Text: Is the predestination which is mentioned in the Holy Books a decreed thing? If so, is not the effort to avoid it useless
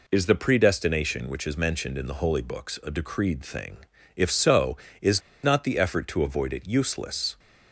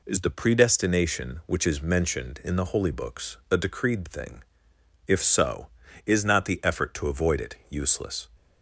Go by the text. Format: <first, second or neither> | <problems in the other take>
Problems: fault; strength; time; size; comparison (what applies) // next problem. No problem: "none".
second | pauses between "is" and "not"; slight; at 5.2 s; 0.22 s long